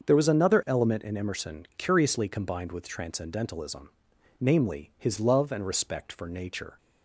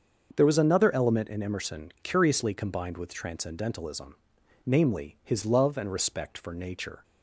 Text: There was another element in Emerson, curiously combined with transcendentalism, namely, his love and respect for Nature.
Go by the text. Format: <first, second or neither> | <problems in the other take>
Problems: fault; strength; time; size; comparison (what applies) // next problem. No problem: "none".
neither | starts louder than the rest; the same in both